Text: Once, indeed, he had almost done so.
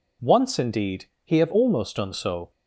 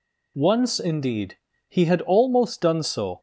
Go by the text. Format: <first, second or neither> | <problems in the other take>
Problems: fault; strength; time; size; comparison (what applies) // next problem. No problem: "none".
second | says "have" for "had"; at 1.3 s